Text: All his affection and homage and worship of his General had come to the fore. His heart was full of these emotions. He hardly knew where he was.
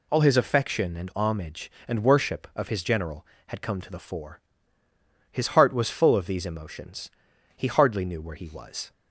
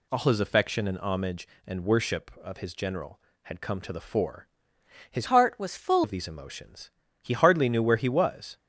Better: first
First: none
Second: changes voice from "heart" to "full"; from 5.2 to 6.0 s; 0.8 s long

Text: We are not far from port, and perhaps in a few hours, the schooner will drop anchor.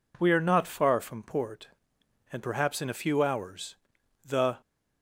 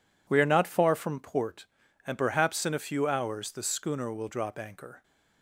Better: second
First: stops before "schooner will drop anchor"; at 4.6 s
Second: none

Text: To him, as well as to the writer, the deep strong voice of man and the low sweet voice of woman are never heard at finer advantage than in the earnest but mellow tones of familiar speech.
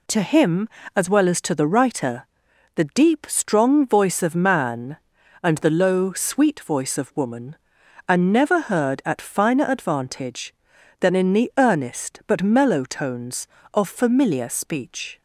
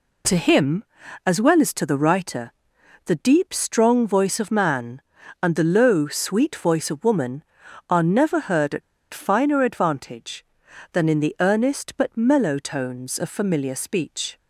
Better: first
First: none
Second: pauses between "at" and "finer"; slight; at 8.8 s; 0.31 s long

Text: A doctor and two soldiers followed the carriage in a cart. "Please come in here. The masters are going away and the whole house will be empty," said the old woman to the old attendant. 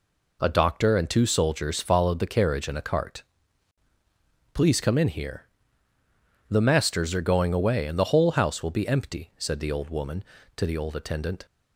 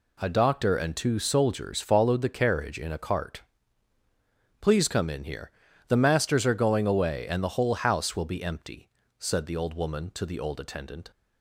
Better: neither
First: none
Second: none

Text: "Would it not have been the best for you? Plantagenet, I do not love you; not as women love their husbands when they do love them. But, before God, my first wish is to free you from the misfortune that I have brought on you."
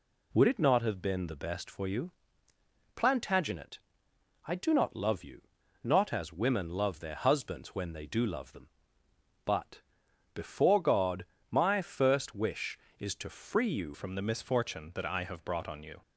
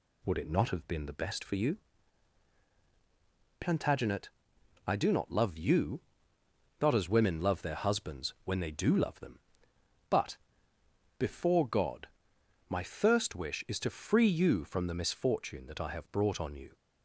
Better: second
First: changes voice at "from"; from 13.9 s on; 2.1 s long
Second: none

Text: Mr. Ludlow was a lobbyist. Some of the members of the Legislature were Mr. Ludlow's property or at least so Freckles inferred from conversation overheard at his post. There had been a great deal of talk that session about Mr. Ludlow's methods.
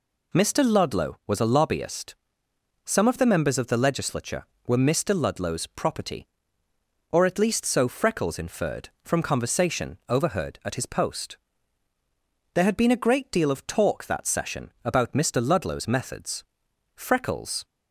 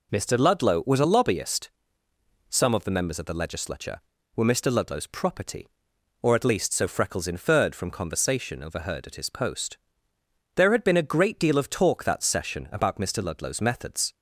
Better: second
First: goes on to say "Freckles"; noticeable; from 16.9 s on; 0.70 s long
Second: none

